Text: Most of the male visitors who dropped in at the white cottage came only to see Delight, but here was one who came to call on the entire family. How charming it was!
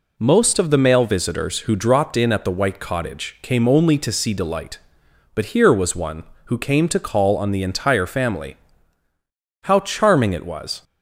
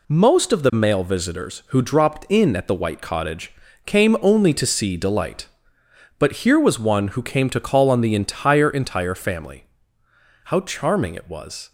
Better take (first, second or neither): first